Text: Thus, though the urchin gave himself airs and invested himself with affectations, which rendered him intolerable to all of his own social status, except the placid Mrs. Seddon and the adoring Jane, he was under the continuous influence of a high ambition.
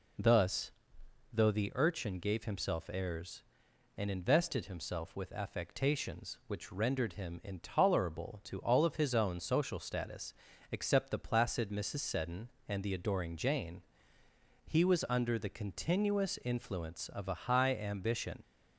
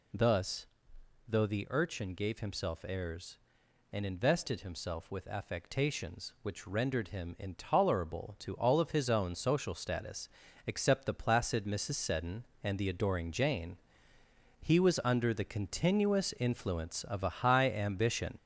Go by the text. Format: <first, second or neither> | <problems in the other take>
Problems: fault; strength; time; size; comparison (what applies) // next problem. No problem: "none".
first | gets louder; noticeable; throughout; 5 dB